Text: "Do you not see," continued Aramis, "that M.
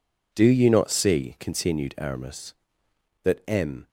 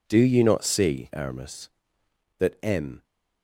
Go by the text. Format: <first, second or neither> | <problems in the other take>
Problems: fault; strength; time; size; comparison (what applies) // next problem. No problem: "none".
first | skips "continued"; at 1.1 s